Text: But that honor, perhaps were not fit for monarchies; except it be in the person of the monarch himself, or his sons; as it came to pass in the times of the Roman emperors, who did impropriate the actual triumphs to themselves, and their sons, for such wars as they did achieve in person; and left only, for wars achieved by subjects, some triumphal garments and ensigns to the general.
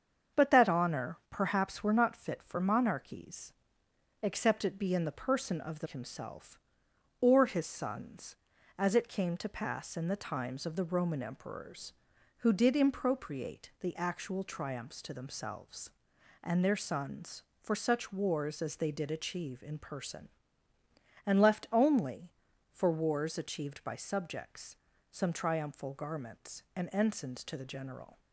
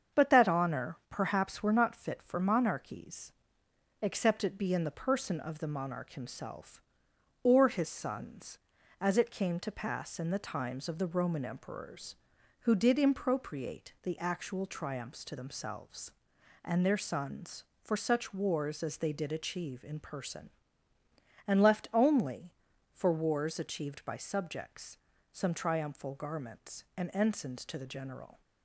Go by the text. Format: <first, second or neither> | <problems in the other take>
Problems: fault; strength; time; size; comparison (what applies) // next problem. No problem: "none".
second | starts louder than the rest; strong; until 1.4 s; 7 dB; strong in the second // skips "monarch"; at 5.8 s